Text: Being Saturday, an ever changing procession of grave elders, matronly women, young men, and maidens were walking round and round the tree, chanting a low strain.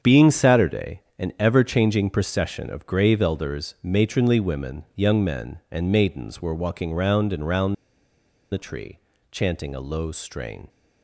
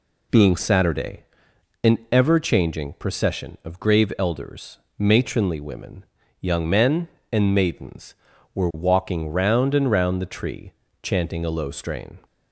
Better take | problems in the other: second | starts louder than the rest; strong; until 1.2 s; 7.5 dB // pauses between "round" and "the"; noticeable; at 7.7 s; 0.77 s long

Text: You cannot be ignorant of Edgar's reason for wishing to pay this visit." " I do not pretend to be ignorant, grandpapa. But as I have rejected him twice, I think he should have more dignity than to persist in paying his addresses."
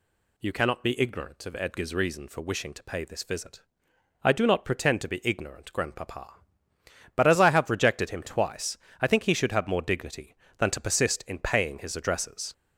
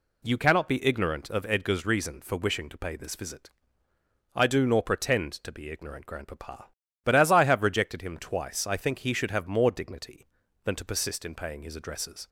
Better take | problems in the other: first | says "nor" for "not"; at 4.6 s

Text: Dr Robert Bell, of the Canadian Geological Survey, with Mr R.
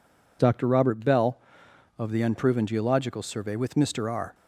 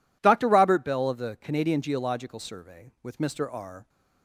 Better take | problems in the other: second | says "Unproven" for "Canadian"; at 2.2 s

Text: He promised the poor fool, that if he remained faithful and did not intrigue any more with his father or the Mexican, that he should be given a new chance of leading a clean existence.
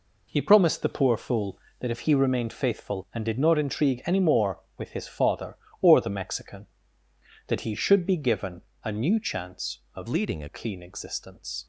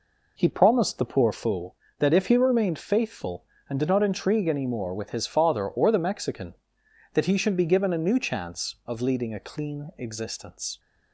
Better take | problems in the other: second | pauses between "given" and "a"; slight; at 8.5 s; 0.24 s long // changes voice from "leading" to "a"; from 10.0 to 10.4 s; 0.4 s long

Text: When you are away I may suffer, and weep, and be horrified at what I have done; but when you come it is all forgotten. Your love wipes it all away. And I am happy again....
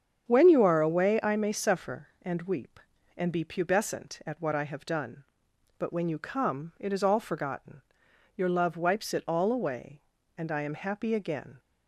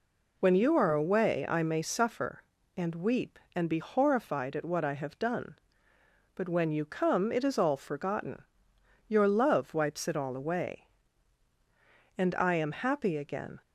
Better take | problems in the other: second | starts louder than the rest; strong; until 1.3 s; 8 dB // says "pubescent" for "horrified"; at 3.4 s

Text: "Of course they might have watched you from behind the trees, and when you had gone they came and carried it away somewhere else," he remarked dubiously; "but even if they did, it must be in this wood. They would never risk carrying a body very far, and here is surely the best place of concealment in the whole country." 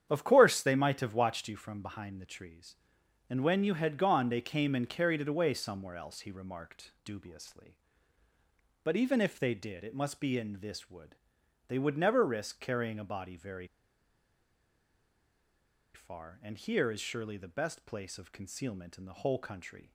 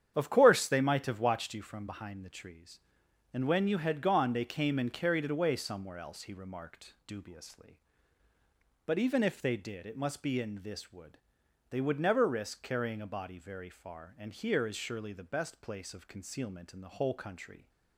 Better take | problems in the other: second | starts louder than the rest; strong; until 1.1 s; 9 dB; strong in the second // pauses between "very" and "far"; strong; at 13.6 s; 2.2 s long

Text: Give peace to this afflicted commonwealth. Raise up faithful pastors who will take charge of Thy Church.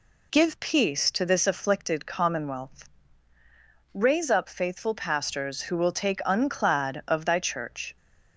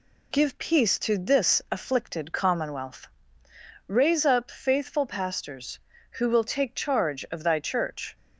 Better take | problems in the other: second | says "unclad" for "charge"; at 6.2 s

